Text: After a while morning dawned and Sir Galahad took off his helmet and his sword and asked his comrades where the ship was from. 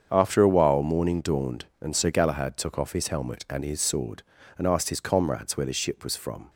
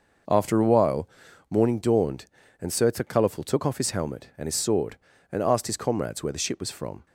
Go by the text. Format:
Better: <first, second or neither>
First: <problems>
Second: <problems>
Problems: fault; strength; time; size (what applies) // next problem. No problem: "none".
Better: first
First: starts louder than the rest; strong; until 1.1 s; 7.5 dB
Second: starts louder than the rest; noticeable; until 1.7 s; 6 dB // pauses between "while" and "morning"; at 1.0 s; 0.42 s long // says "Colorful" for "Galahad"; at 2.9 s